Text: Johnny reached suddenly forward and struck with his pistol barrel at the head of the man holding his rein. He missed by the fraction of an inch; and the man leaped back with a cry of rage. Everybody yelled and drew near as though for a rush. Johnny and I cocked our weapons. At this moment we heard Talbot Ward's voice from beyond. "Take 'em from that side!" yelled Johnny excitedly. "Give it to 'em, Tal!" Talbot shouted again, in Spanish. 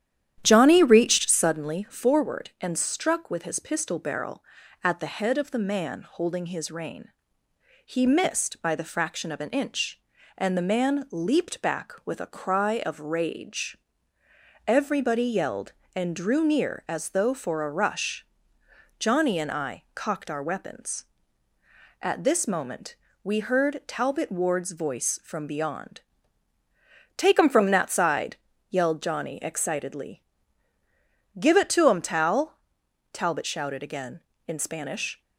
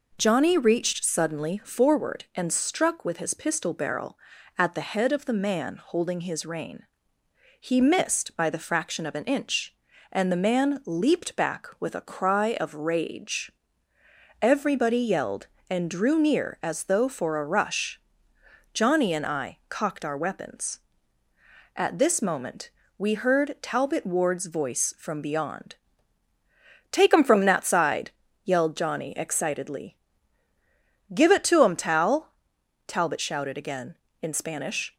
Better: second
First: starts louder than the rest; strong; until 1.5 s; 10.5 dB // pauses between "moment" and "we"; slight; at 22.9 s; 0.28 s long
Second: pauses between "moment" and "we"; slight; at 22.6 s; 0.28 s long

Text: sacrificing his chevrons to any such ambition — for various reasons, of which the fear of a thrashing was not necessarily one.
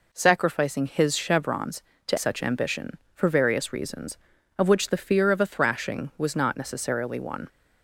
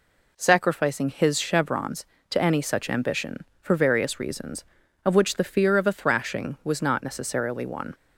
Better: second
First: skips "any"; at 2.1 s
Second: none

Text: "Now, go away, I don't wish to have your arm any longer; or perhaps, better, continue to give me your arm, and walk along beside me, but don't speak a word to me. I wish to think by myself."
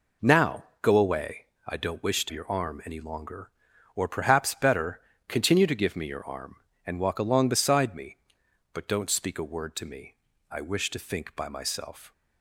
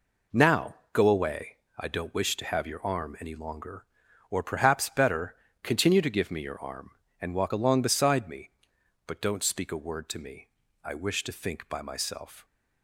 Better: second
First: skips "have"; at 2.3 s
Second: none

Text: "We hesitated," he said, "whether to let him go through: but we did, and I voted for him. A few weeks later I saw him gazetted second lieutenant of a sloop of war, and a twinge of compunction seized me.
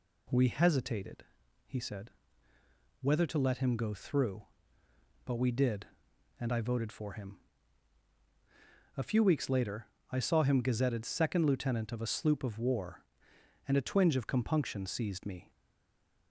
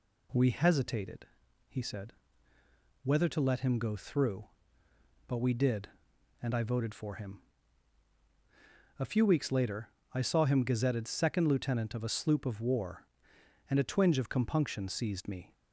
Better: second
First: pauses between "later" and "I"; slight; at 9.8 s; 0.24 s long // stays silent after the last word; slight; from 15.5 s on; 0.8 s long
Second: pauses between "later" and "I"; slight; at 9.8 s; 0.24 s long

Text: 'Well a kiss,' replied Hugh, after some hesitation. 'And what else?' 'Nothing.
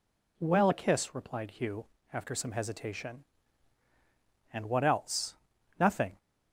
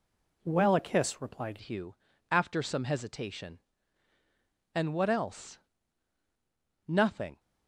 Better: first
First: none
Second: changes voice at "Hugh"; from 1.6 s on; 5.7 s long

